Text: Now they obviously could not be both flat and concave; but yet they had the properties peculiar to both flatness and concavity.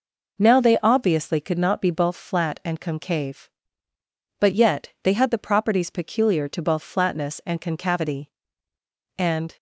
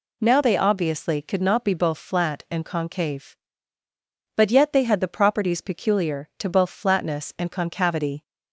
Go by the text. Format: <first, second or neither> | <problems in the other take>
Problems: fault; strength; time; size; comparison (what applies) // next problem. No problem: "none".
second | goes on to say "And"; slight; from 9.1 s on; 0.40 s long